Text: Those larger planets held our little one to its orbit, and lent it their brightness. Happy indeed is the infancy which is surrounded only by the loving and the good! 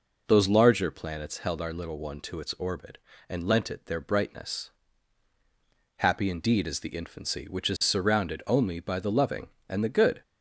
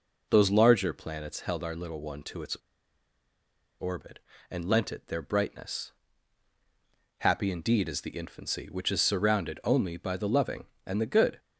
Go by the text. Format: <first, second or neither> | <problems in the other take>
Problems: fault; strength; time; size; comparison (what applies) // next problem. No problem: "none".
first | pauses between "its" and "orbit"; at 2.5 s; 1.2 s long